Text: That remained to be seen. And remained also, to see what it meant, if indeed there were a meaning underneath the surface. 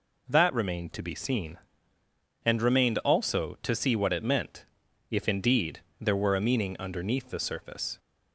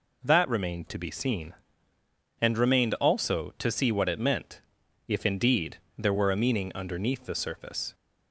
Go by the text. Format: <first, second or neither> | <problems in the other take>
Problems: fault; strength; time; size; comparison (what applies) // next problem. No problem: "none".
neither | pauses between "indeed" and "there"; slight; the same in both